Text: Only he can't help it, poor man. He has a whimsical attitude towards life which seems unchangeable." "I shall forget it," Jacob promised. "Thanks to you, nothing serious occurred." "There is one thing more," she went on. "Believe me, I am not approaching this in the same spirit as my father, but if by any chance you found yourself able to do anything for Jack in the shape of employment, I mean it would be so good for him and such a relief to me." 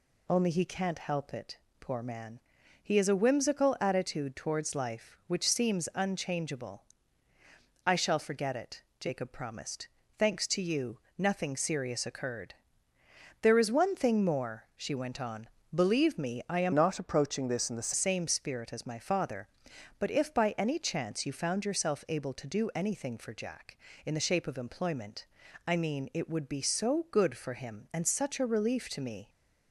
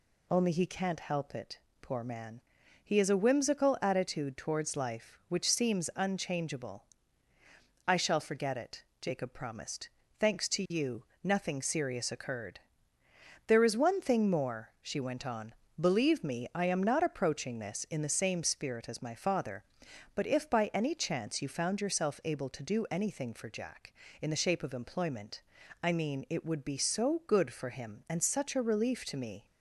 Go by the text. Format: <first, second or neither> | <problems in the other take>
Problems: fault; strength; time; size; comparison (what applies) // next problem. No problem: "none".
second | changes voice from "not" to "the"; from 16.7 to 17.9 s; 1.2 s long